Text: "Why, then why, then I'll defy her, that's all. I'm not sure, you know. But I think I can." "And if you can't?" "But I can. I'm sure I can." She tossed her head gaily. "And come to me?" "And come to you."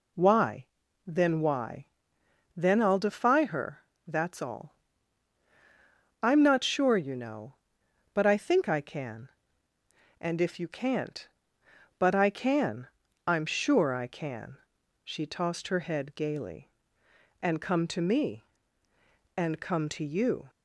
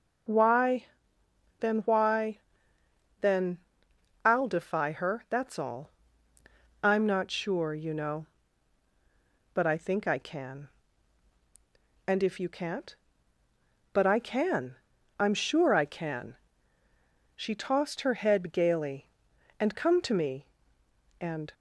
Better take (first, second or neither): first